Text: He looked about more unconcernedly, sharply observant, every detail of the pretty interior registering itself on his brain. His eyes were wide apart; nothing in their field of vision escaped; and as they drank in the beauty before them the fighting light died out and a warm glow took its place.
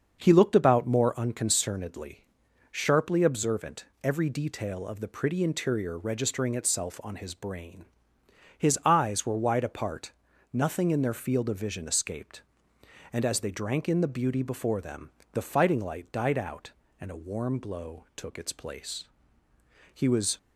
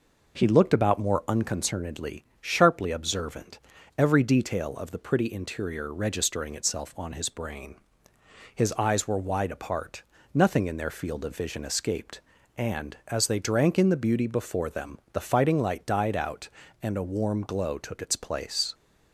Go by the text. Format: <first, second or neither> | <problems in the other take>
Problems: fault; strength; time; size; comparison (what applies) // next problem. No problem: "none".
second | starts louder than the rest; until 1.2 s; 6.5 dB // pauses between "them" and "the"; slight; at 15.0 s; 0.22 s long; slight in the second // goes on to say "He was"; slight; from 19.9 s on; 0.44 s long